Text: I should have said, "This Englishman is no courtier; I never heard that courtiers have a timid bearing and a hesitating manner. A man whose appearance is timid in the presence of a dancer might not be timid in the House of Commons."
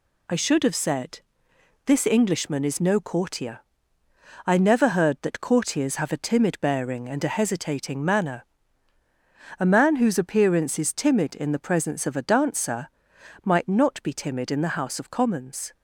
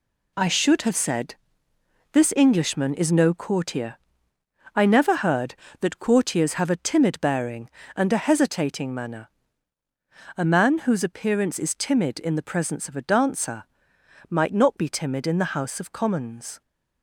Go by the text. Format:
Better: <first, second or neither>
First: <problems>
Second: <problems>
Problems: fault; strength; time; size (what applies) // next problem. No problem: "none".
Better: first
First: pauses between "dancer" and "might"; noticeable; at 12.8 s; 0.56 s long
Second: gets quieter; strong; throughout; 8 dB // pauses between "dancer" and "might"; noticeable; at 13.6 s; 0.64 s long